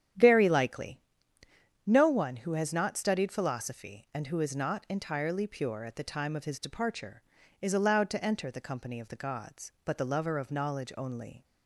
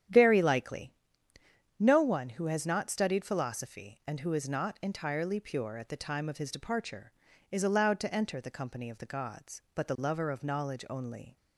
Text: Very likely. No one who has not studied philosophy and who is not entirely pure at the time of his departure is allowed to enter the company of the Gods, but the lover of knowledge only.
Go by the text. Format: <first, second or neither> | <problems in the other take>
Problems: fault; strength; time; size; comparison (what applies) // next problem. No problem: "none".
neither | starts louder than the rest; strong; the same in both